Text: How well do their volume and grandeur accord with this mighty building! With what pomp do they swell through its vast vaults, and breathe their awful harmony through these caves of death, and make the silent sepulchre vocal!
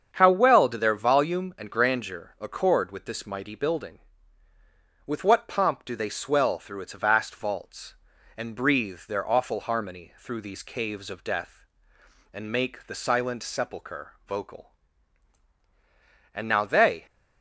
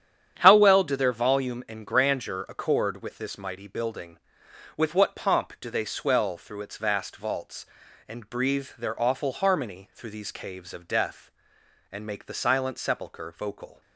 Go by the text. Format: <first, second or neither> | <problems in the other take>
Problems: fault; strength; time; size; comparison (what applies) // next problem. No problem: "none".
second | starts louder than the rest; strong; until 1.1 s; 7.5 dB; strong in the second // goes on to say "And now they"; noticeable; from 16.3 s on; 0.72 s long